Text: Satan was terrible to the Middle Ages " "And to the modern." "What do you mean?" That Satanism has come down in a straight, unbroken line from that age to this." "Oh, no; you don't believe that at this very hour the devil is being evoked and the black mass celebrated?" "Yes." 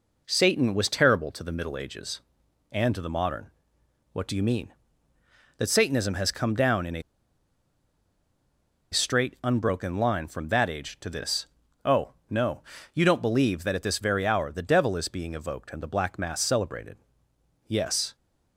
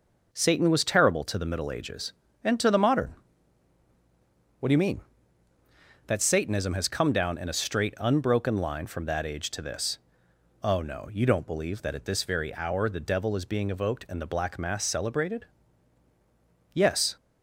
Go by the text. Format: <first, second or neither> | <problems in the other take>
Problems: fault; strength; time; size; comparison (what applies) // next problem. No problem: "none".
second | pauses between "a" and "straight"; strong; at 7.0 s; 1.9 s long